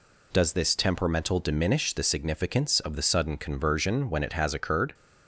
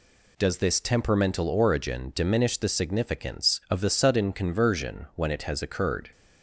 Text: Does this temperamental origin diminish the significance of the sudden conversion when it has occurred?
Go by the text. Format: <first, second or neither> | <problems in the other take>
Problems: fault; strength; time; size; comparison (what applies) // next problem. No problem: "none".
second | skips "origin"; at 1.3 s